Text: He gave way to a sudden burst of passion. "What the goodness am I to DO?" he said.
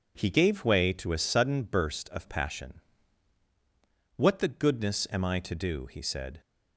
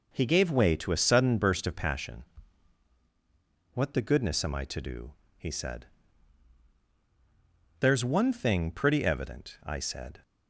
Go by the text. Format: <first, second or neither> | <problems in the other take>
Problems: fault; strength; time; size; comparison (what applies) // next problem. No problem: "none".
first | goes on to say "There's one thing pretty evident I said"; strong; from 7.8 s on; 2.4 s long